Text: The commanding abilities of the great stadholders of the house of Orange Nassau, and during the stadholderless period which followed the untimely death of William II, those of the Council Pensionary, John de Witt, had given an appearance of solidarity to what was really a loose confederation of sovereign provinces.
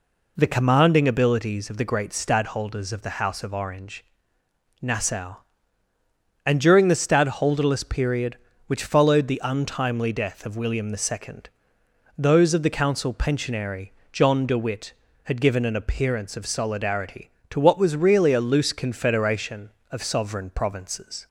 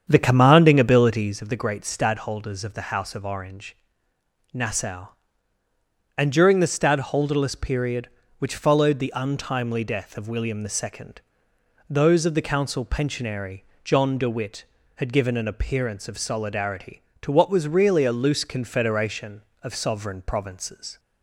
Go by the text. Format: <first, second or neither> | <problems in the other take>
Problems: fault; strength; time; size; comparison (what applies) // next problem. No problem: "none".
first | starts louder than the rest; strong; until 1.5 s; 8 dB // pauses between "Orange" and "Nassau"; noticeable; at 3.7 s; 0.78 s long; noticeable in the first